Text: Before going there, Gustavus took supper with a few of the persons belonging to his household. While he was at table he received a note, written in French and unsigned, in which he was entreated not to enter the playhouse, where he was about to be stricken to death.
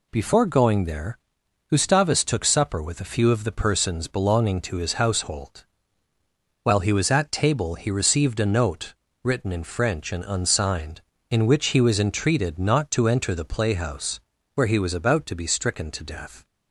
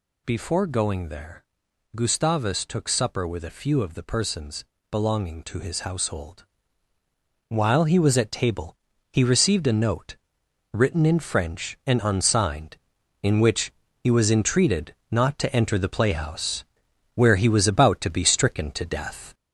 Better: first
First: none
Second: gets louder; noticeable; throughout; 4.5 dB // pauses between "persons" and "belonging"; slight; at 4.6 s; 0.26 s long // pauses between "table" and "he"; slight; at 8.7 s; 0.36 s long // pauses between "which" and "he"; slight; at 13.6 s; 0.32 s long // pauses between "entreated" and "not"; slight; at 14.9 s; 0.18 s long

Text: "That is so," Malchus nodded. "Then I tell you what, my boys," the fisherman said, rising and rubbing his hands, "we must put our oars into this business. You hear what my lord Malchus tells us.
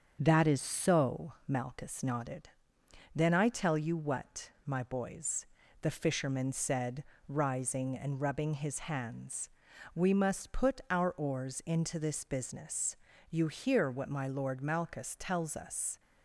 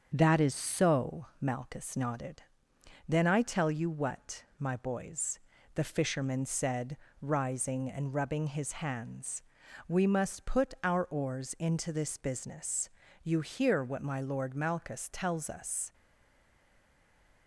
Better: first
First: starts louder than the rest; strong; until 1.2 s; 7 dB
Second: starts louder than the rest; strong; until 1.1 s; 7 dB // stays silent after the last word; noticeable; from 15.9 s on; 1.5 s long

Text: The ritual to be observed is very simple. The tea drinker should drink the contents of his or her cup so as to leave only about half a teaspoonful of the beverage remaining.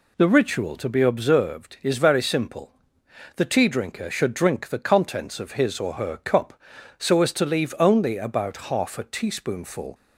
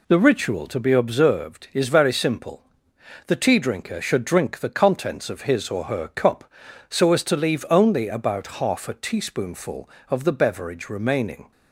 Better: second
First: stops before "of the beverage remaining"; at 9.9 s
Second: none

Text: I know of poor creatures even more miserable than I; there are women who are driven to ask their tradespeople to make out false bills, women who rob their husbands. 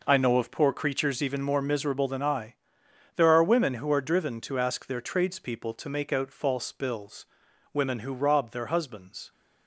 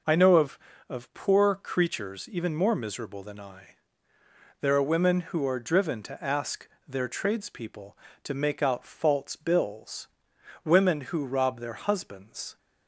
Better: first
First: none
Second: says "of" twice; at 0.8 s // pauses between "ask" and "their"; slight; at 6.6 s; 0.18 s long

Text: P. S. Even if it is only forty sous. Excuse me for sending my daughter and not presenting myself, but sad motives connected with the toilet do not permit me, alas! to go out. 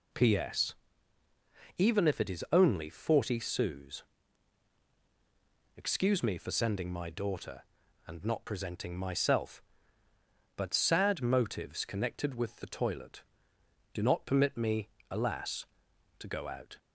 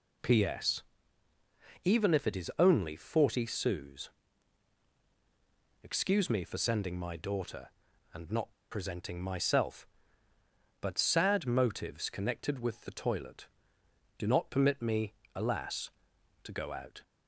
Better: first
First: none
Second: pauses between "not" and "presenting"; slight; at 8.5 s; 0.19 s long

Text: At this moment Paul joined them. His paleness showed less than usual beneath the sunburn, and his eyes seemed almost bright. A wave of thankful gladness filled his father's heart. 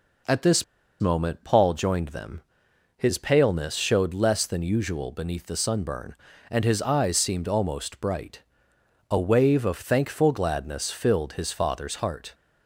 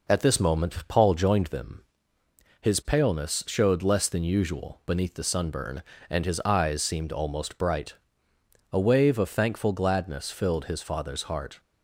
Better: second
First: pauses between "this" and "moment"; slight; at 0.6 s; 0.36 s long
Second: none

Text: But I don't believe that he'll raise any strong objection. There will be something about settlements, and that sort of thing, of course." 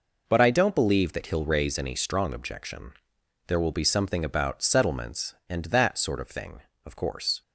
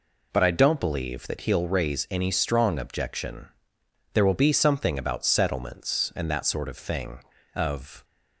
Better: first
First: none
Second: stops before "course"; at 8.0 s

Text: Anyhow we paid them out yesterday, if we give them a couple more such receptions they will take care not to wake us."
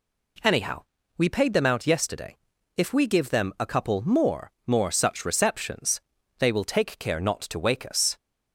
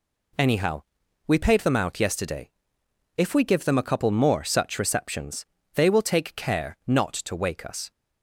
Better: second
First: pauses between "Anyhow" and "we"; slight; at 0.8 s; 0.36 s long // says "more" twice; at 4.6 s // pauses between "receptions" and "they"; at 5.9 s; 0.40 s long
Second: pauses between "Anyhow" and "we"; at 0.8 s; 0.44 s long // pauses between "receptions" and "they"; slight; at 5.4 s; 0.28 s long

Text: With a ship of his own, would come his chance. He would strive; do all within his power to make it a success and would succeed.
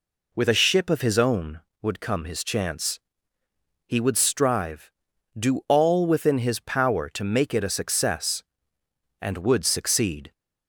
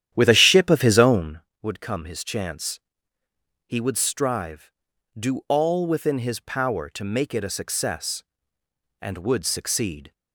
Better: first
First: none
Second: starts louder than the rest; strong; until 1.4 s; 11 dB

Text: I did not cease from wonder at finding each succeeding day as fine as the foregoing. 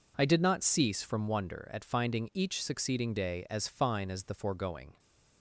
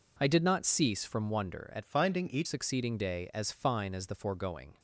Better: first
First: none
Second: changes voice from "finding" to "each"; from 1.8 to 2.4 s; 0.6 s long

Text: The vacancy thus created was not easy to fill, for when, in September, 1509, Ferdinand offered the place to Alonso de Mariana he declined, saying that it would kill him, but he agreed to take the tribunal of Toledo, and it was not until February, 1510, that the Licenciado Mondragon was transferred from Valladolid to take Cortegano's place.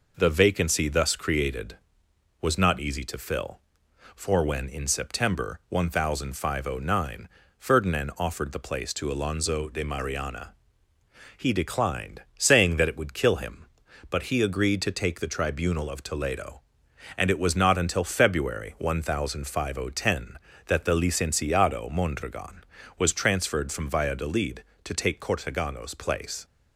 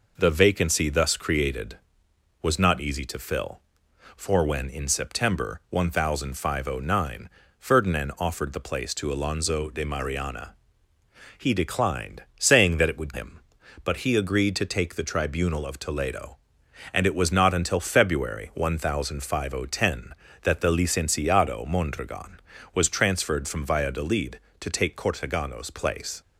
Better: first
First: pauses between "Mariana" and "he"; noticeable; at 10.5 s; 0.84 s long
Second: pauses between "Mariana" and "he"; noticeable; at 10.5 s; 0.84 s long // skips "kill"; at 13.1 s

